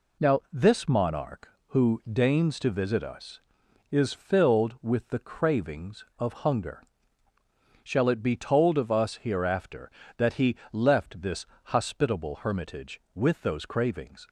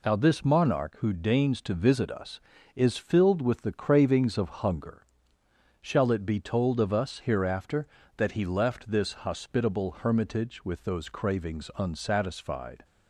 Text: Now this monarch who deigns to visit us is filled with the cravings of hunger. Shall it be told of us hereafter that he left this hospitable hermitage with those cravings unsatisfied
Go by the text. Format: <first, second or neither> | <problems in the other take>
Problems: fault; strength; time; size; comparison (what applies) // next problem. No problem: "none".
second | pauses between "he" and "left"; slight; at 10.5 s; 0.16 s long // pauses between "this" and "hospitable"; slight; at 11.4 s; 0.18 s long // stops before "unsatisfied"; at 14.2 s